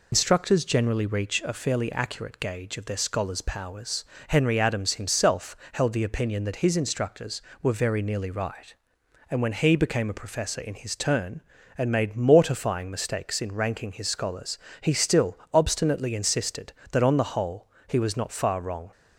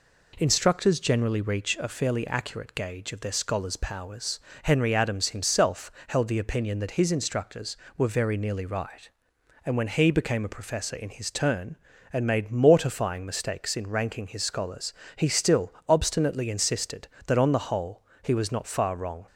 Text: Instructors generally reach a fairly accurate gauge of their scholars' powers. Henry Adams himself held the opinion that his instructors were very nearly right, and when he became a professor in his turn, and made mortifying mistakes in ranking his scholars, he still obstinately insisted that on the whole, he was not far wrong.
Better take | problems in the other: second | loses the start of "Instructors"; at 0.1 s; 140 ms // pauses between "himself" and "held"; slight; at 5.5 s; 0.16 s long; slight in the second // pauses between "still" and "obstinately"; slight; at 15.3 s; 0.16 s long; slight in the second

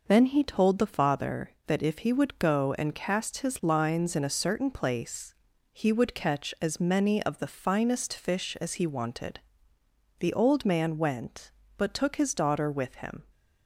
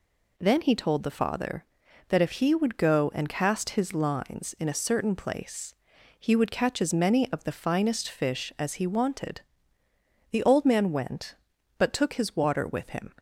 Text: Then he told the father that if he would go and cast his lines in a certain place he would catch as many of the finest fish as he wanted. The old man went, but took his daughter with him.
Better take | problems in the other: first | pauses between "place" and "he"; noticeable; at 5.7 s; 0.46 s long; slight in the first // says "water" for "daughter"; at 12.3 s

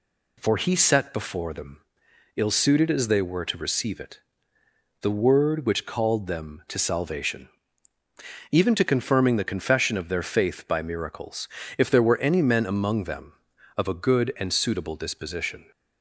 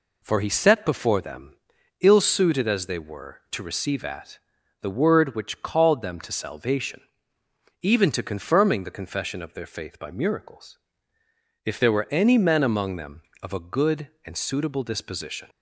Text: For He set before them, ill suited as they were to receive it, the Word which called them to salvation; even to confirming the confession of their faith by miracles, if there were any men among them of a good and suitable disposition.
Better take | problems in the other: first | says "at" for "it"; at 4.0 s

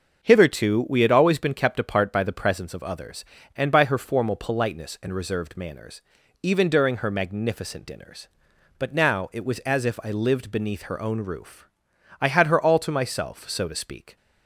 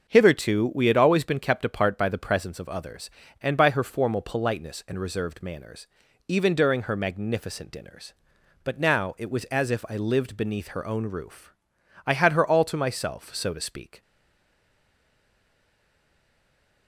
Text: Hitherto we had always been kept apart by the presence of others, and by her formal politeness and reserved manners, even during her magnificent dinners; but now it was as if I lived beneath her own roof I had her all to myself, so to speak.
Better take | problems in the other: first | starts louder than the rest; until 1.1 s; 6.5 dB; also in the first // pauses between "roof" and "I"; noticeable; at 11.5 s; 0.52 s long; noticeable in the first // stays silent after the last word; strong; from 14.0 s on; 2.8 s long

